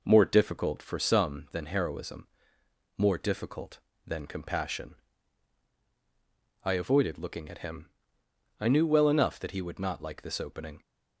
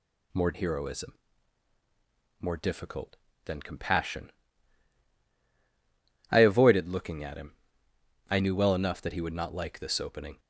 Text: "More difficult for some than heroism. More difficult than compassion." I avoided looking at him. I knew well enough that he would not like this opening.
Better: first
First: none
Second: skips "difficult for some than"; at 0.5 s

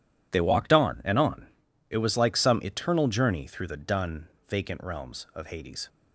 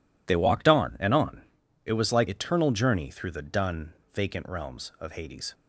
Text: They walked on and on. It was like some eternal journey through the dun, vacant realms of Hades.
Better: first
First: none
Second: skips "some"; at 2.2 s

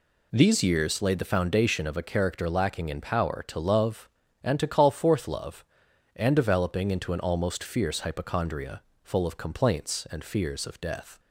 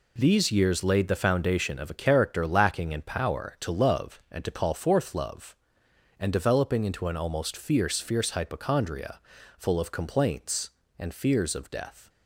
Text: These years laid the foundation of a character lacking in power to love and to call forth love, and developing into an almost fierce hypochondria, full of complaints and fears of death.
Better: first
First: none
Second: says "fierce" twice; at 8.0 s

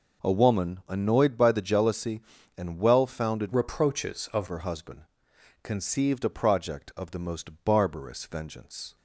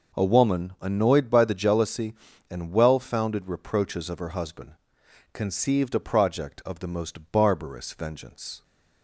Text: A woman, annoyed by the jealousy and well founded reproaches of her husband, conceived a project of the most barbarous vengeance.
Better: second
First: changes voice from "reproaches" to "of"; from 3.5 to 4.4 s; 0.9 s long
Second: none

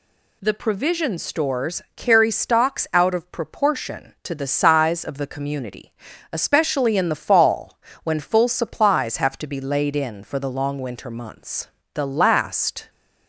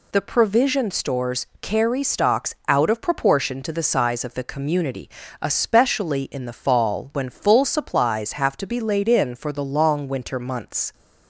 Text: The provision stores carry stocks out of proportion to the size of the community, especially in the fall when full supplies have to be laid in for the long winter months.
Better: second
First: pauses between "stores" and "carry"; slight; at 1.8 s; 0.16 s long // pauses between "fall" and "when"; slight; at 7.7 s; 0.26 s long // goes on to say "The last"; noticeable; from 11.9 s on; 0.96 s long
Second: none

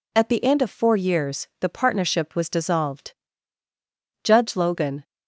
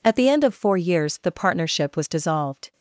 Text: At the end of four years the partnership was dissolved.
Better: second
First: goes on to say "Judge Logan"; noticeable; from 4.2 s on; 0.80 s long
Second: none

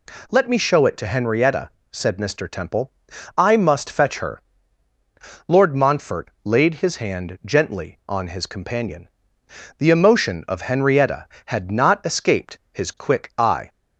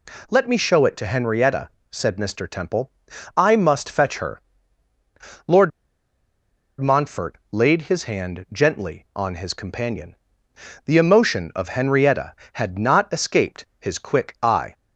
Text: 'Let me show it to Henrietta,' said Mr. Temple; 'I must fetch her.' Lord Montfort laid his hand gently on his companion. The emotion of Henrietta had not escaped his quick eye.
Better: first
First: none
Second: pauses between "Lord" and "Montfort"; at 5.7 s; 1.1 s long

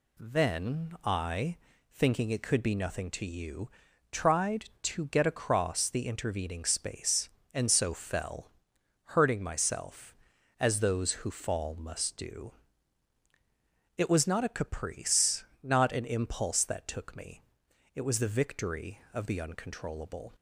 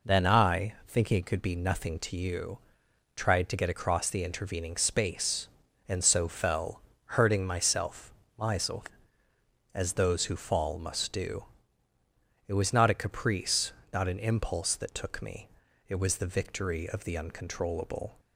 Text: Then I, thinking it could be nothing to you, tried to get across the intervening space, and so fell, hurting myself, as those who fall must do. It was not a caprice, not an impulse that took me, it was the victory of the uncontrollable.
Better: first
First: none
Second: says "myself" twice; at 8.3 s

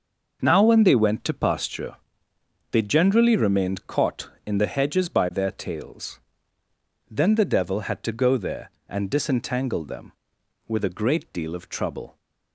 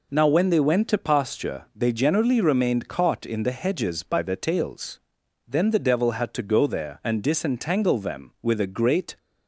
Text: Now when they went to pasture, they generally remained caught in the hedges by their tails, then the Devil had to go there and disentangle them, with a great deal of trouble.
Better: first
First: none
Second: stops before "deal of trouble"; at 9.1 s

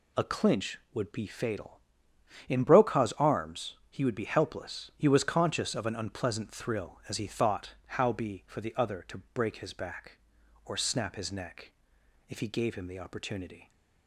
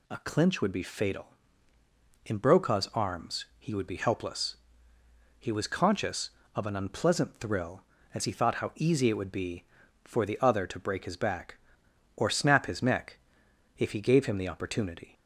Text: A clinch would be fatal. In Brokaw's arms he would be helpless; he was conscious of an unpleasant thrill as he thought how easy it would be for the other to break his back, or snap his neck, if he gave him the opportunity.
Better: second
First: skips "easy it would"; at 8.1 s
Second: none

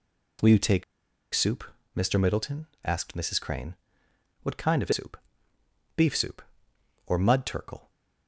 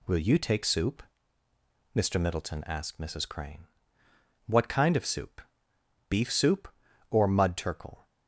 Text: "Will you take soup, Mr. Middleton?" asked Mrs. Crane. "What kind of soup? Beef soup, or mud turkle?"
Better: second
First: pauses between "take" and "soup"; noticeable; at 0.8 s; 0.50 s long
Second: none

